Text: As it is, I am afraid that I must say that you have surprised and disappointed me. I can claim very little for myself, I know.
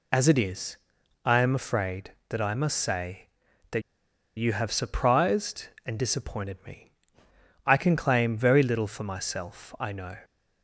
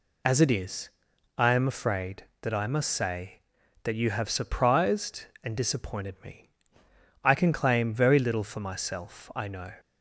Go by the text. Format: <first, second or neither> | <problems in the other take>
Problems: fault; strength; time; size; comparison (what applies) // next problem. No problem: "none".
second | pauses between "that" and "you"; noticeable; at 3.8 s; 0.55 s long